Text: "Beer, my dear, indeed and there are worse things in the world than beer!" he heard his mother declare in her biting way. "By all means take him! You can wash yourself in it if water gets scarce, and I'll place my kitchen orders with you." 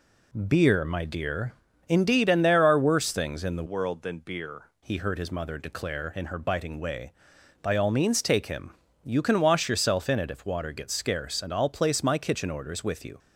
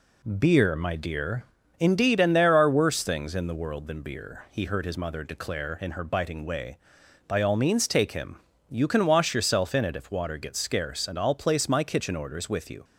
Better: second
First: changes voice from "world" to "beer"; from 3.6 to 4.6 s; 1.0 s long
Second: none

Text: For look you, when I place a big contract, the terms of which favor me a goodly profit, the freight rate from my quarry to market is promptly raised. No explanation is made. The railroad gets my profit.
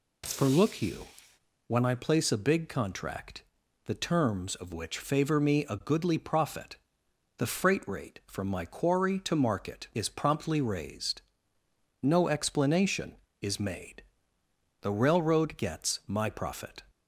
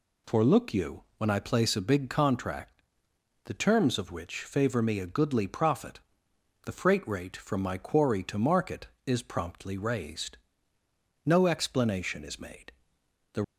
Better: first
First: none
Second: stops before "railroad gets my profit"; at 13.4 s

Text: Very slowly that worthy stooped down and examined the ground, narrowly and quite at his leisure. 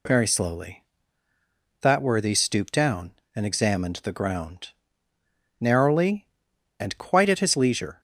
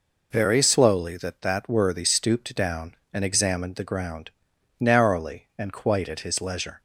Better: first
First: none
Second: says "that" twice; at 1.4 s

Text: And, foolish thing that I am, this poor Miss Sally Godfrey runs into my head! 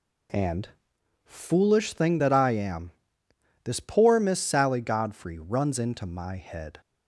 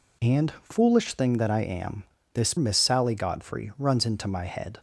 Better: first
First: none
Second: skips "poor"; at 2.5 s

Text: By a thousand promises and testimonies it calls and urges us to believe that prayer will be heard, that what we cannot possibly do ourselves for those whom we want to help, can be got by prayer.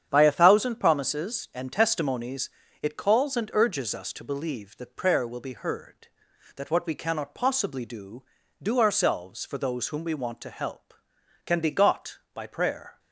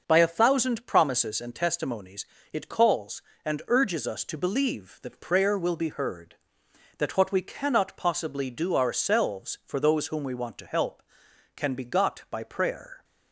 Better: second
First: starts louder than the rest; strong; until 1.1 s; 8.5 dB // pauses between "testimonies" and "it"; slight; at 2.4 s; 0.32 s long // says "do" twice; at 8.6 s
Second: starts louder than the rest; noticeable; until 1.0 s; 6 dB // pauses between "testimonies" and "it"; slight; at 2.2 s; 0.26 s long

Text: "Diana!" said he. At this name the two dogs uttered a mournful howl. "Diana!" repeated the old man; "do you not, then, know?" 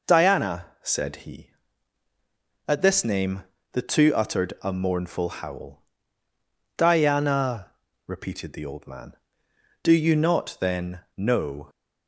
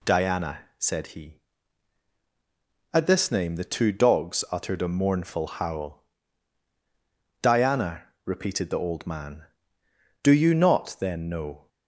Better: second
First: pauses between "name" and "the"; slight; at 3.4 s; 0.28 s long // skips "dogs"; at 4.1 s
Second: none

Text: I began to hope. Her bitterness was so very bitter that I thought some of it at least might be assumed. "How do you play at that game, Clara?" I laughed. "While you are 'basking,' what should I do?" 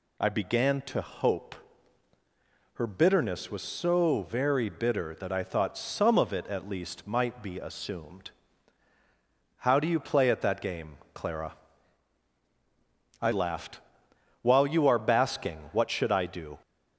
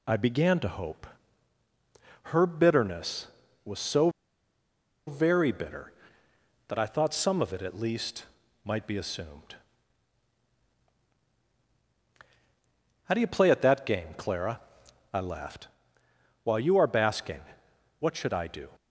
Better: first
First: none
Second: pauses between "so" and "very"; noticeable; at 4.0 s; 0.97 s long // pauses between "least" and "might"; at 8.2 s; 0.40 s long

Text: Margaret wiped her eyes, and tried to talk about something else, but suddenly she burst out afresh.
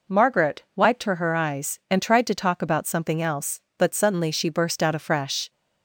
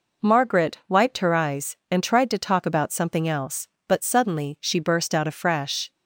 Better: second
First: says "her" twice; at 1.1 s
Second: none

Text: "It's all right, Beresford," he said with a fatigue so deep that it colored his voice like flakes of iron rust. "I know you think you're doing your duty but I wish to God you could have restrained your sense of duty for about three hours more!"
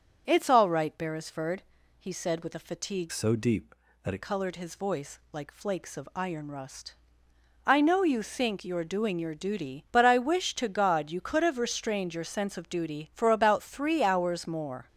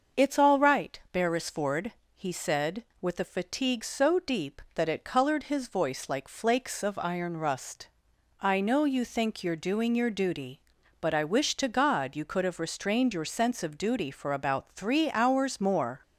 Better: second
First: starts louder than the rest; until 1.2 s; 7 dB // changes voice from "so" to "it"; from 3.1 to 4.2 s; 1.1 s long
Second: starts louder than the rest; until 1.3 s; 6.5 dB

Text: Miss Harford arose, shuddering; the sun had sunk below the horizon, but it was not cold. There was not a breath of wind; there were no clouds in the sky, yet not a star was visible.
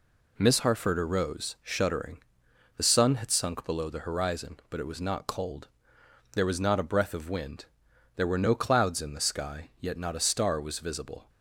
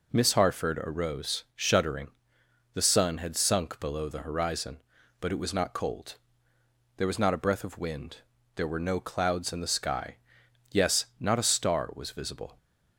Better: first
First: none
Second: says "yes" for "yet"; at 10.7 s

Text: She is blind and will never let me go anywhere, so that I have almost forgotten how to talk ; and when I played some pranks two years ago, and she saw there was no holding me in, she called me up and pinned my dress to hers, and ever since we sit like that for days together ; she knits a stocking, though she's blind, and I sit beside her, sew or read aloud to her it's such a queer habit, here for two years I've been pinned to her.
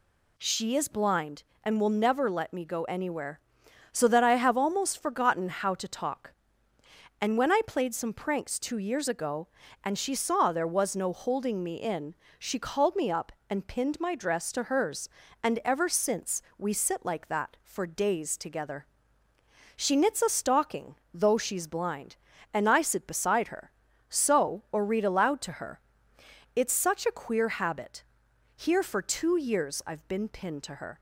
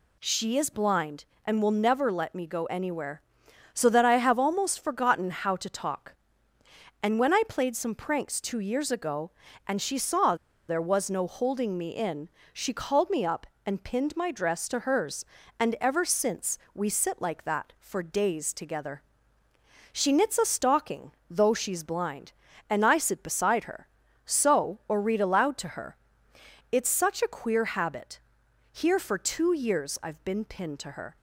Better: first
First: pauses between "since" and "we"; slight; at 16.4 s; 0.16 s long // pauses between "her" and "it's"; noticeable; at 25.7 s; 0.76 s long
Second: pauses between "saw" and "there"; slight; at 10.3 s; 0.33 s long // pauses between "since" and "we"; slight; at 16.5 s; 0.16 s long // pauses between "her" and "it's"; noticeable; at 25.9 s; 0.76 s long

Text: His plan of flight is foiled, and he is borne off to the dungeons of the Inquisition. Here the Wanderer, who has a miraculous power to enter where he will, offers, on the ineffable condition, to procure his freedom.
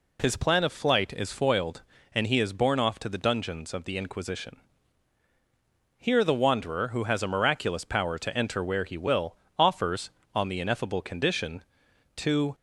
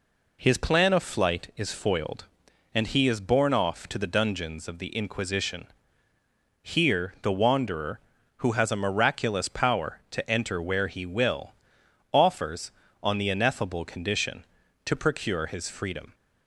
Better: second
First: stops before "procure his freedom"; at 12.5 s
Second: none

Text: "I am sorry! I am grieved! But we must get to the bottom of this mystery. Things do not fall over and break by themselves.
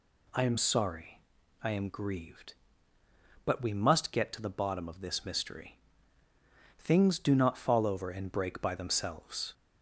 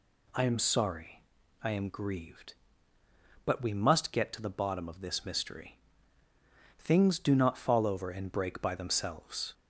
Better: neither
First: none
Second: none

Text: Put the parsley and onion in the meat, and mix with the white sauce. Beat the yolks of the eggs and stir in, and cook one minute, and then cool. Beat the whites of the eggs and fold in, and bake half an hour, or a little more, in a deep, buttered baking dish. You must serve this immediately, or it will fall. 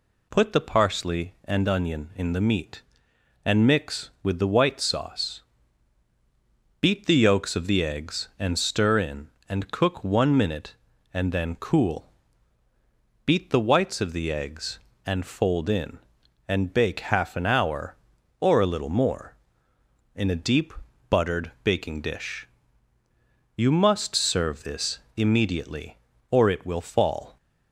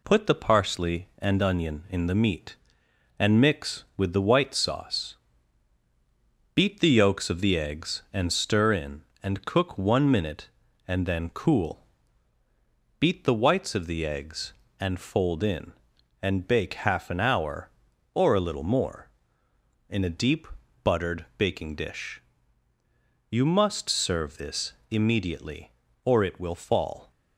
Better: first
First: pauses between "this" and "immediately"; slight; at 24.9 s; 0.16 s long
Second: gets quieter; slight; throughout; 2.5 dB // pauses between "this" and "immediately"; slight; at 24.7 s; 0.16 s long

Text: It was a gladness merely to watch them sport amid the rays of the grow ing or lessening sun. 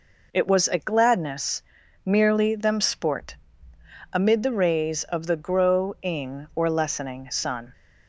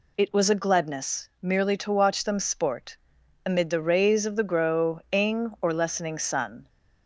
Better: second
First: pauses between "gladness" and "merely"; at 1.6 s; 0.44 s long // skips "to watch"; at 2.5 s // pauses between "sport" and "amid"; noticeable; at 3.3 s; 0.78 s long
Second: pauses between "sport" and "amid"; noticeable; at 2.9 s; 0.48 s long

